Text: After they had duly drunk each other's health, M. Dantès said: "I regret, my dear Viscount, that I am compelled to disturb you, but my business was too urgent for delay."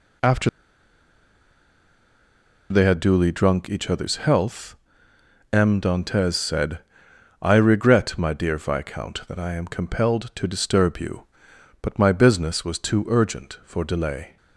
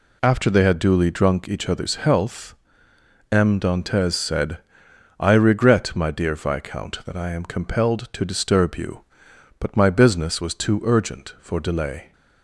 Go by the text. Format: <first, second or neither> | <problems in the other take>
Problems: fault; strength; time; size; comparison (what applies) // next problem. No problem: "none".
second | pauses between "After" and "they"; strong; at 0.4 s; 2.2 s long